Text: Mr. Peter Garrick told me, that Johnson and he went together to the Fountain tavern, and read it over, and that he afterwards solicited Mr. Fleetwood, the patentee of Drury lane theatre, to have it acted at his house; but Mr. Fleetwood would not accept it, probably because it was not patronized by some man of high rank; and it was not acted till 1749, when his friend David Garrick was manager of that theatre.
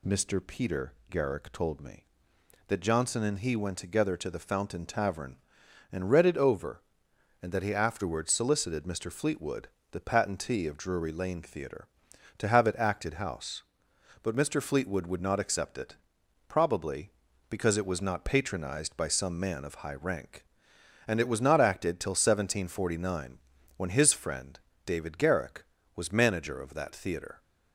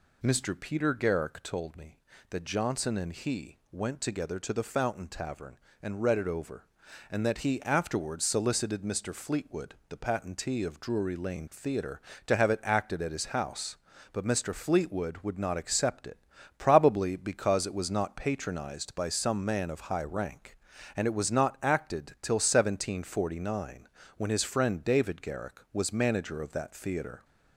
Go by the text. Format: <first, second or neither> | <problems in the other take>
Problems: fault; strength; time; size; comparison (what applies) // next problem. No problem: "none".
second | pauses between "Peter" and "Garrick"; slight; at 0.9 s; 0.16 s long // skips "at his"; at 13.1 s // pauses between "friend" and "David"; slight; at 24.5 s; 0.26 s long